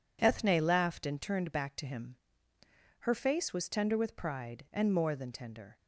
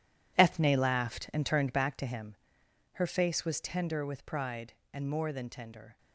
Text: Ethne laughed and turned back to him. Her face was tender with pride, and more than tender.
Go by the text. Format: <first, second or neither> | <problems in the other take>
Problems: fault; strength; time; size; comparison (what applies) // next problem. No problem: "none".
first | gets quieter; strong; throughout; 12 dB